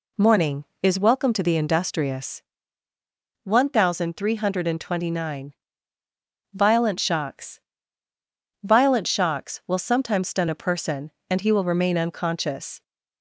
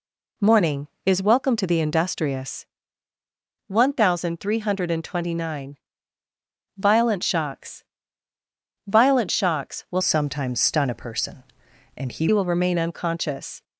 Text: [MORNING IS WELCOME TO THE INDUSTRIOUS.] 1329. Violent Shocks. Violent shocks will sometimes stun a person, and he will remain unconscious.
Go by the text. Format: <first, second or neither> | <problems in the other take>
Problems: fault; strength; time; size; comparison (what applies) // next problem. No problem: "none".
first | changes voice from "sometimes" to "he"; from 10.0 to 12.2 s; 2.2 s long